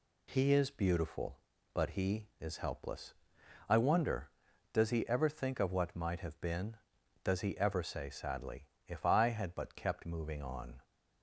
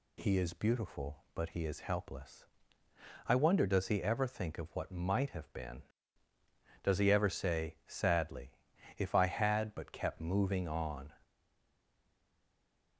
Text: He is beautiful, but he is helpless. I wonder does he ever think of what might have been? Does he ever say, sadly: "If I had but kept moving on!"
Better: first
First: none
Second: stays silent after the last word; noticeable; from 11.2 s on; 1.7 s long

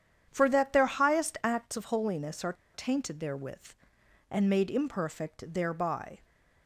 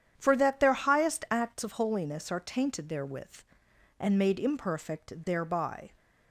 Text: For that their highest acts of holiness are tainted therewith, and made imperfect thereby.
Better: second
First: starts louder than the rest; strong; until 1.3 s; 9 dB // pauses between "are" and "tainted"; slight; at 2.5 s; 0.21 s long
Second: starts louder than the rest; strong; until 1.1 s; 9 dB

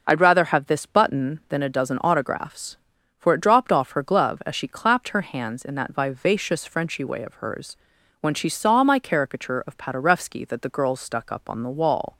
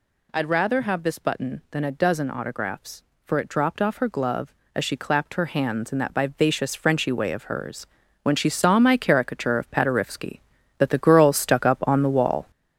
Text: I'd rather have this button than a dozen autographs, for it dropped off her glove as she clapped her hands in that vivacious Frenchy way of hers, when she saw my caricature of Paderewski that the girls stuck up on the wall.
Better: first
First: none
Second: gets louder; noticeable; throughout; 6 dB

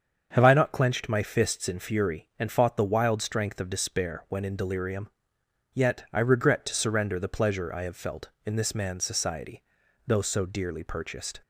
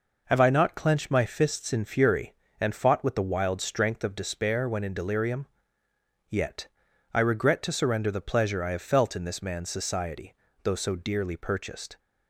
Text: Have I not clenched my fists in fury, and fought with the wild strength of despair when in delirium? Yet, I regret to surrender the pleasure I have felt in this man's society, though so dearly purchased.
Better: second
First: starts louder than the rest; until 1.3 s; 7 dB // skips "with"; at 2.7 s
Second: none

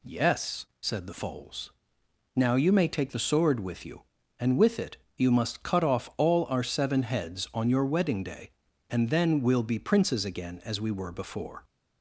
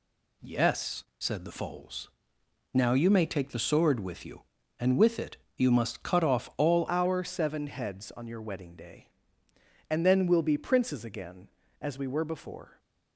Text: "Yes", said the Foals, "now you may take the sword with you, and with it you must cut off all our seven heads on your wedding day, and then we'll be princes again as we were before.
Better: first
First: pauses between "it" and "you"; slight; at 4.9 s; 0.20 s long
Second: pauses between "it" and "you"; slight; at 5.3 s; 0.20 s long // changes voice at "our"; from 6.8 s on; 5.9 s long

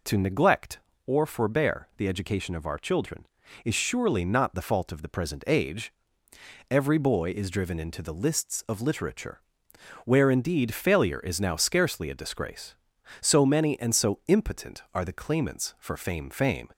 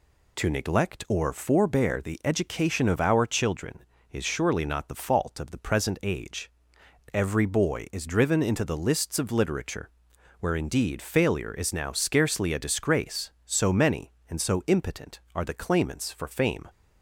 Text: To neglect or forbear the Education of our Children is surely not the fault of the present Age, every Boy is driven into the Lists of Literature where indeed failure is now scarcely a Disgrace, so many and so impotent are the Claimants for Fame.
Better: second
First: pauses between "Literature" and "where"; noticeable; at 9.3 s; 0.64 s long // says "Fame" twice; at 16.2 s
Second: pauses between "Literature" and "where"; noticeable; at 9.8 s; 0.50 s long

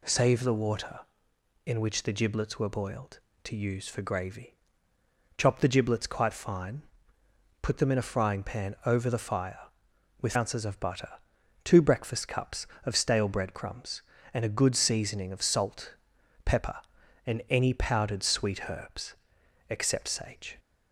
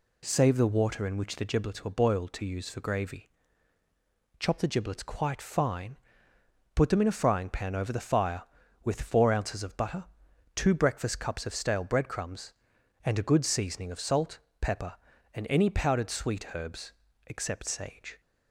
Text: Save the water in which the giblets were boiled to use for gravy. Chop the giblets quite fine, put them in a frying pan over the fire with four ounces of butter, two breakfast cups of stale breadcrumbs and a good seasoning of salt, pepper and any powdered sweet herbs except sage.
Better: second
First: skips "four"; at 10.3 s // pauses between "herbs" and "except"; noticeable; at 19.1 s; 0.56 s long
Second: pauses between "herbs" and "except"; slight; at 16.9 s; 0.34 s long

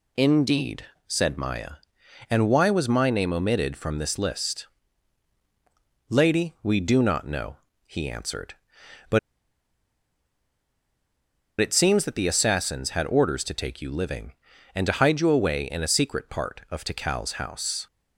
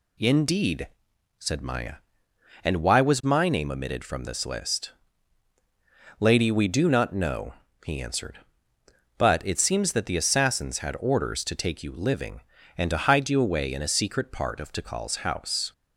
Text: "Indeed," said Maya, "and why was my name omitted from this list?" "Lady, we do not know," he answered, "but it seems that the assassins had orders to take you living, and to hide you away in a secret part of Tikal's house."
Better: second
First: pauses between "but" and "it"; strong; at 9.1 s; 2.4 s long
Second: none

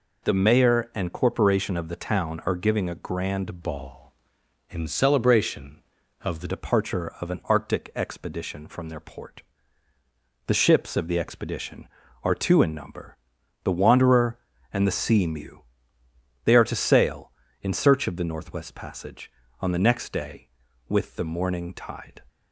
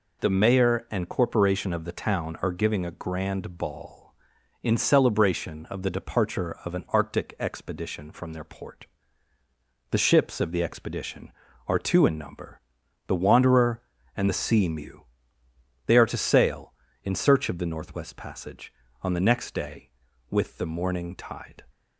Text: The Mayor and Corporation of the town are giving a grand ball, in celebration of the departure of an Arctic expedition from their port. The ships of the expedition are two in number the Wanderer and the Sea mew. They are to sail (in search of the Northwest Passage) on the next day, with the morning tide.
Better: second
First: changes voice from "ball" to "the"; from 3.6 to 6.4 s; 2.8 s long // pauses between "number" and "the"; noticeable; at 13.1 s; 0.46 s long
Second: pauses between "number" and "the"; noticeable; at 12.6 s; 0.46 s long

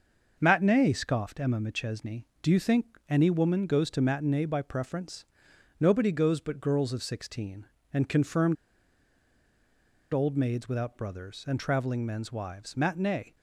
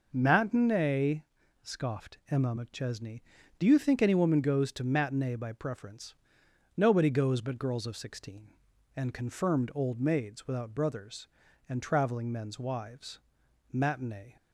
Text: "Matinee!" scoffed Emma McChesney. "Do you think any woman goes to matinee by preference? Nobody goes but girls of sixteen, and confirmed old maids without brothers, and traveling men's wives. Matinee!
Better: second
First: starts louder than the rest; noticeable; until 1.4 s; 6 dB // pauses between "confirmed" and "old"; strong; at 8.5 s; 1.5 s long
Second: none

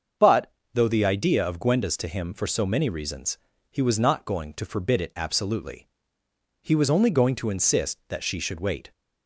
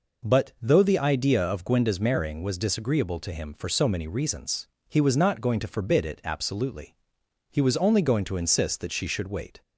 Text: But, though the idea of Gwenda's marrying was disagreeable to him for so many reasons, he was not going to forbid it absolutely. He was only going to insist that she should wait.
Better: second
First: starts louder than the rest; until 1.4 s; 7 dB // skips "marrying was disagreeable"; at 1.9 s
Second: none

